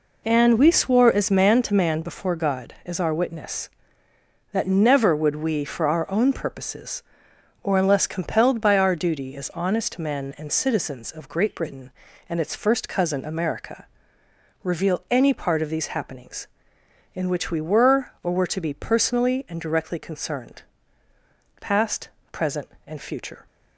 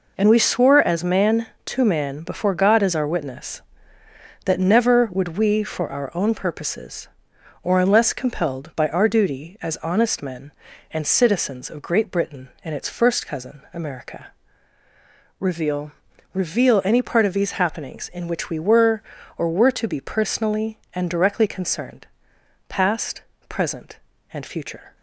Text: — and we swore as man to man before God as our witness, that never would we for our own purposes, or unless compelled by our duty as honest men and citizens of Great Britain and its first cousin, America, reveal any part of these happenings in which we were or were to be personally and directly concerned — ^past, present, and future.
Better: first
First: none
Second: says "reveal" twice; at 16.3 s

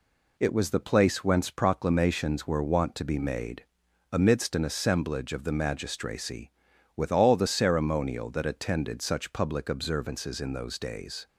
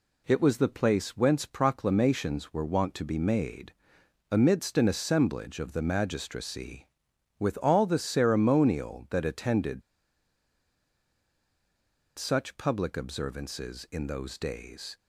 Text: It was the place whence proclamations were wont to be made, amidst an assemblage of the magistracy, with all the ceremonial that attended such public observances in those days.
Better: first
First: none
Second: pauses between "attended" and "such"; strong; at 9.8 s; 2.3 s long

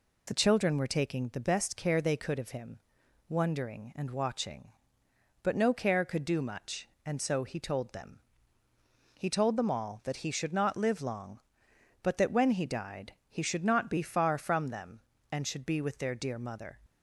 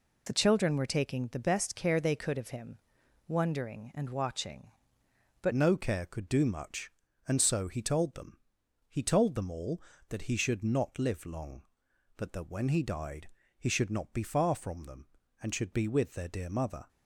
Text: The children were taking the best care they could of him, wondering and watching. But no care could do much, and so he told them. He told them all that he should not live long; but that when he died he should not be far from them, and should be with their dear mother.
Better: first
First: pauses between "died" and "he"; slight; at 13.1 s; 0.18 s long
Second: changes voice at "no"; from 5.5 s on; 11.3 s long // pauses between "died" and "he"; slight; at 13.2 s; 0.30 s long

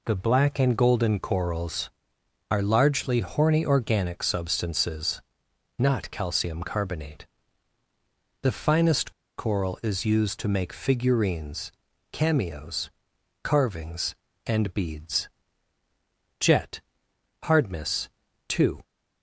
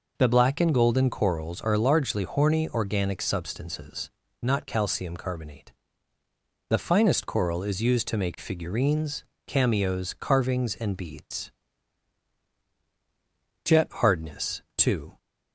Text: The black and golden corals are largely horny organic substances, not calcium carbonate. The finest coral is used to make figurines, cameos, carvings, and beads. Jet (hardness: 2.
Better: second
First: pauses between "finest" and "coral"; slight; at 9.1 s; 0.25 s long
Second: none

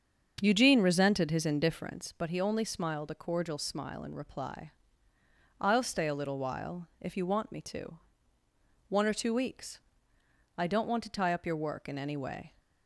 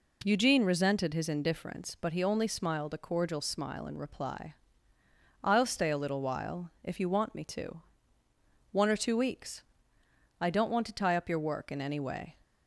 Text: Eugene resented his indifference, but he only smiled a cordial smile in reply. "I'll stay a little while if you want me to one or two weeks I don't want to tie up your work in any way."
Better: second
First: starts louder than the rest; strong; until 2.0 s; 7 dB // pauses between "to" and "one"; noticeable; at 7.9 s; 0.88 s long // pauses between "weeks" and "I"; noticeable; at 9.8 s; 0.76 s long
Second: pauses between "to" and "one"; noticeable; at 7.8 s; 0.88 s long // pauses between "weeks" and "I"; noticeable; at 9.6 s; 0.76 s long

